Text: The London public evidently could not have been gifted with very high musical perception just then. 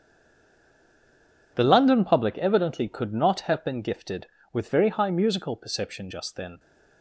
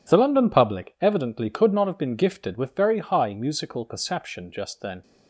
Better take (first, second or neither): second